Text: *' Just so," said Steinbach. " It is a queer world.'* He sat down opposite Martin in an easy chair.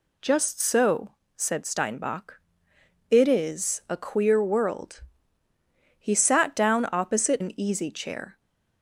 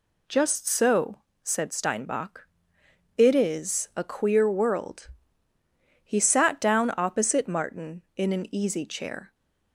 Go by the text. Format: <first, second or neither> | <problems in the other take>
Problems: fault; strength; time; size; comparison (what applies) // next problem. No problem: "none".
second | skips "Martin in"; at 7.4 s